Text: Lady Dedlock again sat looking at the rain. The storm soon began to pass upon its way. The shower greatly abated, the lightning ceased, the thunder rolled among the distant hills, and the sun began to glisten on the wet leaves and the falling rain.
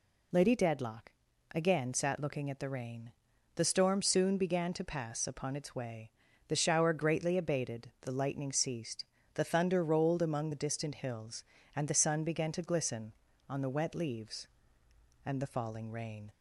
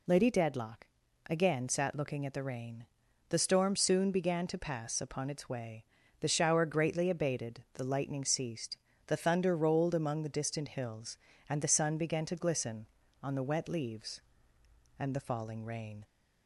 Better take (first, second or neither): neither